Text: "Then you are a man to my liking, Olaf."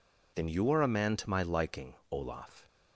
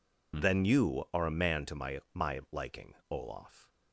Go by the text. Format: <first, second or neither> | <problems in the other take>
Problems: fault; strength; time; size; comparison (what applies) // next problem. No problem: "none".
first | says "my" twice; at 2.1 s